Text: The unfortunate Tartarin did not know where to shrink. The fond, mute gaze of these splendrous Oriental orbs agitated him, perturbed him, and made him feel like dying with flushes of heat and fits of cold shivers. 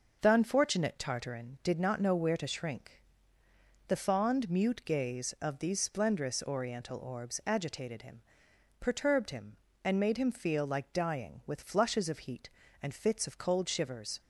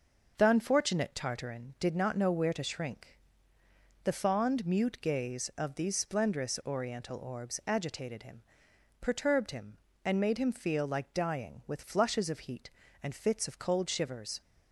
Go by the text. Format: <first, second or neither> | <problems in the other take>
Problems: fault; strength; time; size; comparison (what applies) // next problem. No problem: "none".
neither | none